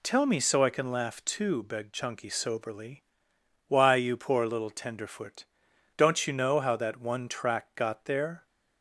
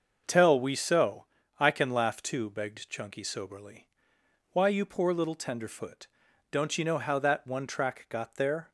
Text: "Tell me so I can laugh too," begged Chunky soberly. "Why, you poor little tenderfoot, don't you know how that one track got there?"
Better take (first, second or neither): first